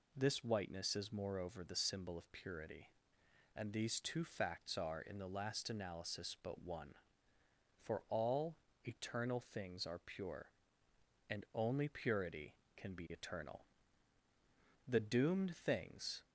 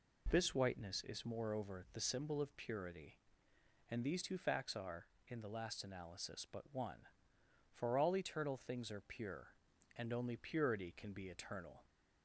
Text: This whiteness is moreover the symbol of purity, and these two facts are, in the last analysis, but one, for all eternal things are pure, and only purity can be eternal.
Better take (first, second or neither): second